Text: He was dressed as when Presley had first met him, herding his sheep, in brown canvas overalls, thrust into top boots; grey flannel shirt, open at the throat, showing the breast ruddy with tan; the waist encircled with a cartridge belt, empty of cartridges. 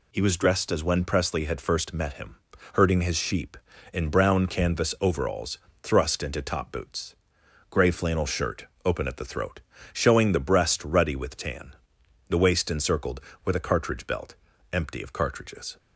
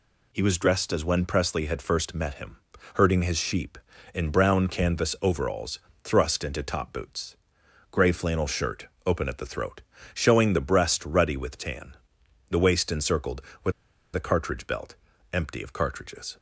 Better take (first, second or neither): first